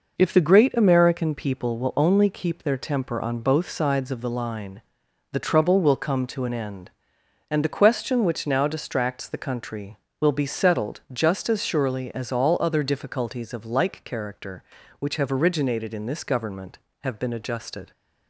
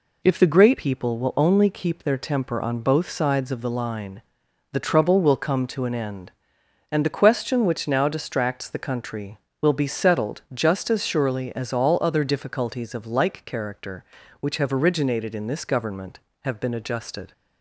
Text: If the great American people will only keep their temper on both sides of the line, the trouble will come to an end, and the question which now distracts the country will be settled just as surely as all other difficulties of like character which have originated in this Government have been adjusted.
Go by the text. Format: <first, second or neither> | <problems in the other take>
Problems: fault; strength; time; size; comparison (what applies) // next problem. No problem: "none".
first | skips "American"; at 0.7 s